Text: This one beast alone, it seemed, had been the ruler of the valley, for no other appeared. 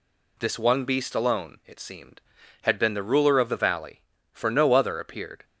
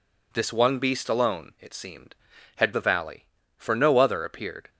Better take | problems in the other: first | skips "been the ruler of"; at 2.7 s

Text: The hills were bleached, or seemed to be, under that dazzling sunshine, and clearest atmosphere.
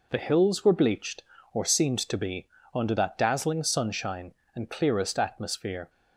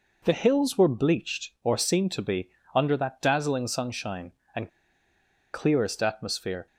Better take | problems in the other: first | pauses between "and" and "clearest"; noticeable; at 4.6 s; 0.83 s long

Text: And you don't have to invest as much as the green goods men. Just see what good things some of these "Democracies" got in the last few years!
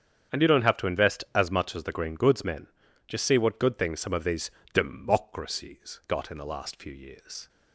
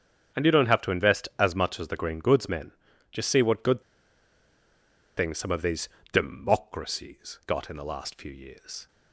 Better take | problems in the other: first | starts louder than the rest; strong; until 1.4 s; 8 dB; strong in the first // pauses between "good" and "things"; strong; at 3.8 s; 1.3 s long // pauses between "these" and "Democracies"; slight; at 5.8 s; 0.24 s long; slight in the first

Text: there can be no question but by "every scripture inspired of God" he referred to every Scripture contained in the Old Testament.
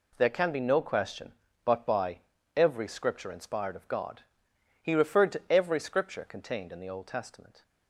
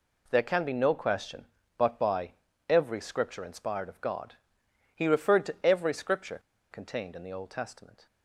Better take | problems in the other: first | pauses between "by" and "every"; at 2.3 s; 0.38 s long; also in the first // pauses between "God" and "he"; noticeable; at 4.3 s; 0.58 s long; noticeable in the first // pauses between "Scripture" and "contained"; slight; at 6.4 s; 0.31 s long

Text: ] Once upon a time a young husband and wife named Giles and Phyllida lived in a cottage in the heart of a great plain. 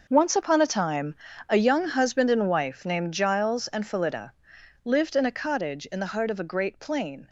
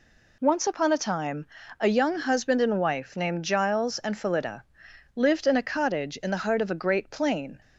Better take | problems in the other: second | gets quieter; strong; throughout; 13.5 dB // pauses between "time" and "a"; slight; at 1.1 s; 0.36 s long; slight in the second // pauses between "Phyllida" and "lived"; noticeable; at 4.3 s; 0.54 s long; noticeable in the second

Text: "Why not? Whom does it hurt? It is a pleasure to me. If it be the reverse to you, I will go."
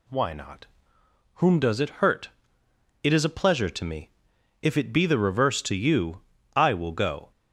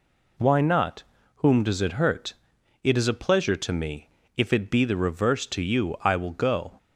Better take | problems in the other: neither | none

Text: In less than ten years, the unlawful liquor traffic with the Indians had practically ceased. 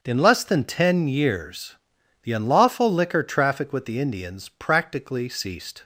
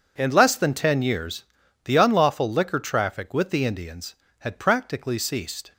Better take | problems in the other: second | starts louder than the rest; until 1.0 s; 7 dB // skips "had"; at 4.4 s

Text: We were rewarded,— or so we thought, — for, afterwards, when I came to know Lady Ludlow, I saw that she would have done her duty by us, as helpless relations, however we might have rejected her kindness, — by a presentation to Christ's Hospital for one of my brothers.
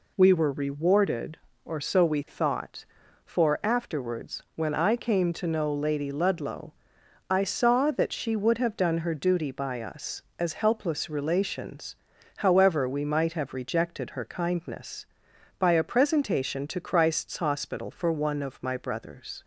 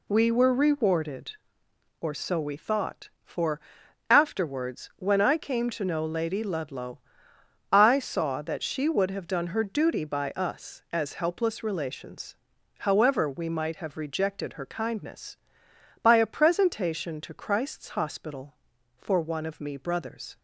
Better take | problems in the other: first | says "me" for "my"; at 19.5 s

